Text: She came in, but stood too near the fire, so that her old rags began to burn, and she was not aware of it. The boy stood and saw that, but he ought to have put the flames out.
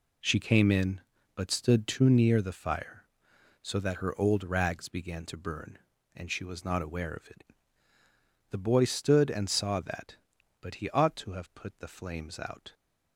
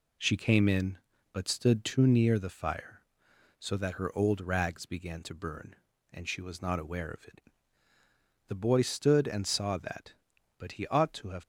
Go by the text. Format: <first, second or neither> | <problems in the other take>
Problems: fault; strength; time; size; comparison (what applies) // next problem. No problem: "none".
first | stops before "put the flames out"; at 11.4 s